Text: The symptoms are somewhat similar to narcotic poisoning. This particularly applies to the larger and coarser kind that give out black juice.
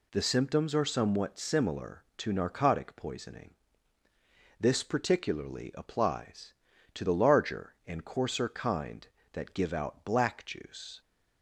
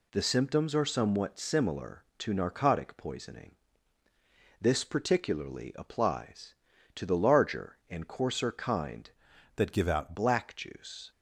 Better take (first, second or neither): first